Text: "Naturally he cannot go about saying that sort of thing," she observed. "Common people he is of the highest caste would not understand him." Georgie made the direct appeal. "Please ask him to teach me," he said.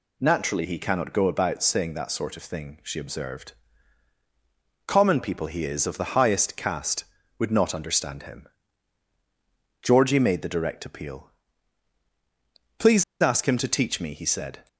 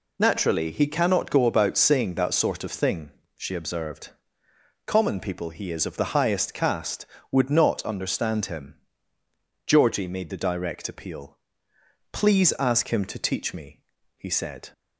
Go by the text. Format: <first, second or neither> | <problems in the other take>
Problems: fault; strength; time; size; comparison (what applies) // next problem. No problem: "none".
second | pauses between "Please" and "ask"; slight; at 13.0 s; 0.18 s long